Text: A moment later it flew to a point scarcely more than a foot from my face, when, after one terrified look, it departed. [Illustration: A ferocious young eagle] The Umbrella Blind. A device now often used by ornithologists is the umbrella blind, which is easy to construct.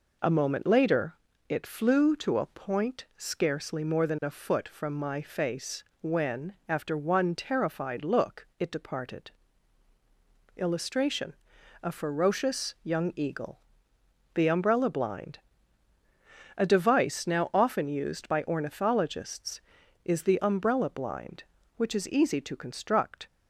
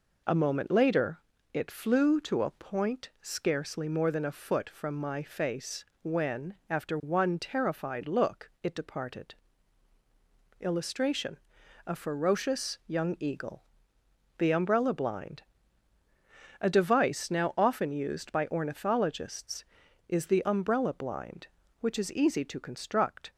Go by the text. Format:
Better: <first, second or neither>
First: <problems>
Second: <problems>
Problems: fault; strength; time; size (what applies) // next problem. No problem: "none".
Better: neither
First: pauses between "later" and "it"; slight; at 1.1 s; 0.36 s long // pauses between "eagle" and "The"; noticeable; at 13.6 s; 0.74 s long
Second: pauses between "later" and "it"; slight; at 1.1 s; 0.36 s long // pauses between "eagle" and "The"; noticeable; at 13.6 s; 0.74 s long